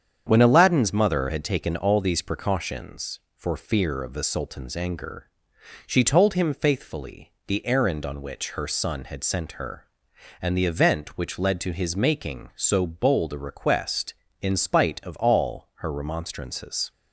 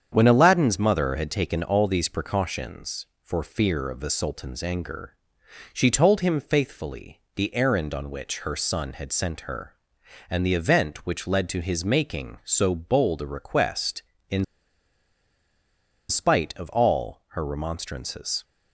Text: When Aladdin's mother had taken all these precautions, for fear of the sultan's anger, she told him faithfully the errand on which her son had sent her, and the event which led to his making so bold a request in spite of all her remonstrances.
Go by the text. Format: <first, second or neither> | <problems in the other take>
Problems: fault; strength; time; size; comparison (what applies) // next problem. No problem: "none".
first | starts louder than the rest; strong; until 1.1 s; 8 dB; strong in the first // pauses between "in" and "spite"; strong; at 14.4 s; 1.6 s long